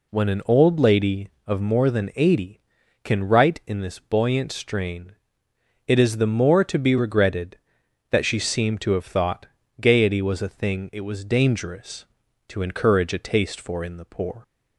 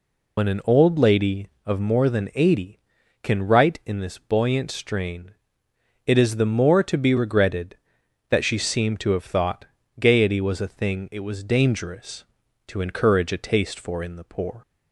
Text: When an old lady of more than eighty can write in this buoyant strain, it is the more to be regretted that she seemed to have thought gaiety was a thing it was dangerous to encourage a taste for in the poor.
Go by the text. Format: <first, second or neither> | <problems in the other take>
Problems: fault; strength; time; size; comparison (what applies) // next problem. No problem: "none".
first | loses the start of "When"; at 0.3 s; 80 ms // pauses between "thought" and "gaiety"; slight; at 9.6 s; 0.34 s long; slight in the first